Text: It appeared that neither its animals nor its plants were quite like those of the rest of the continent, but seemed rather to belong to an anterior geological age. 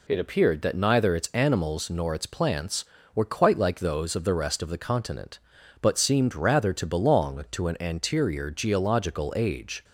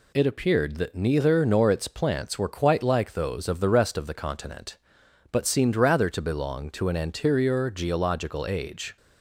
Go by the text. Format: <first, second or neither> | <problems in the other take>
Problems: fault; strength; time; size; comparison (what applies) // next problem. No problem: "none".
first | skips "its animals"; at 1.4 s